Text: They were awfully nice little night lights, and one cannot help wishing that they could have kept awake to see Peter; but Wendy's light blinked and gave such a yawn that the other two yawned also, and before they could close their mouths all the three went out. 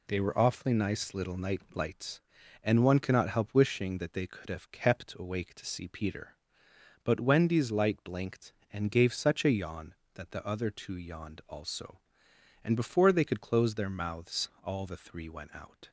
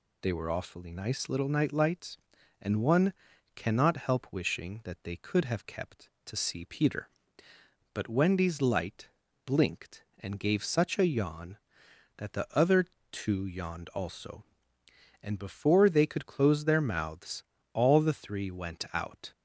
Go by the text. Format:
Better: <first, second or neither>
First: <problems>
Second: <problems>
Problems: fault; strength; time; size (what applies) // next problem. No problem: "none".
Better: first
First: none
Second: pauses between "one" and "cannot"; at 3.1 s; 0.42 s long // skips "awake"; at 6.1 s // pauses between "light" and "blinked"; at 9.0 s; 0.37 s long // pauses between "other" and "two"; slight; at 12.8 s; 0.28 s long // pauses between "mouths" and "all"; slight; at 17.4 s; 0.28 s long